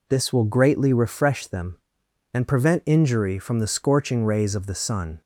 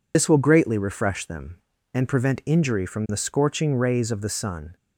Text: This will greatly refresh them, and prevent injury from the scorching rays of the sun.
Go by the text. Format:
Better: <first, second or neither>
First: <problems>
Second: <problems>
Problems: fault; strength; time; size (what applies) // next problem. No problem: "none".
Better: first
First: none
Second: loses the start of "This"; at 0.1 s; 70 ms